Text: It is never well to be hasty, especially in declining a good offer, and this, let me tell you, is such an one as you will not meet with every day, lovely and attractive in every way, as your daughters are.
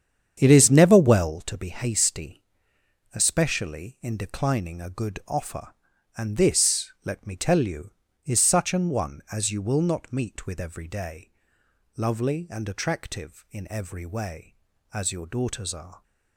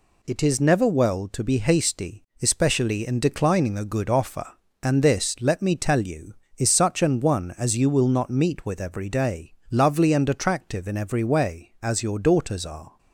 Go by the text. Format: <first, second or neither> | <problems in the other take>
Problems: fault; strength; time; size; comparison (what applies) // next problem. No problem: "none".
second | starts louder than the rest; strong; until 1.5 s; 8 dB